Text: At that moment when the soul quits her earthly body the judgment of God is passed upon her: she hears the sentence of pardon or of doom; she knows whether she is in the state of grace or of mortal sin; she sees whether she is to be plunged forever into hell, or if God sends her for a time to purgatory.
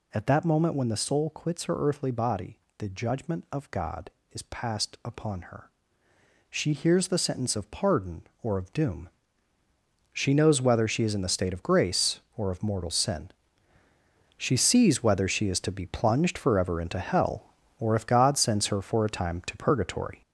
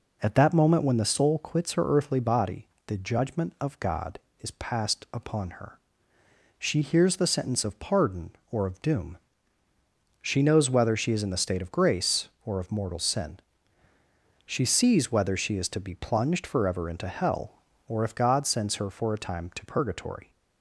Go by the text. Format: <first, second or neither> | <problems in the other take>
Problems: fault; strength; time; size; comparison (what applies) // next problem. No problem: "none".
second | gets louder; noticeable; throughout; 6 dB // pauses between "body" and "the"; slight; at 2.5 s; 0.22 s long; slight in the second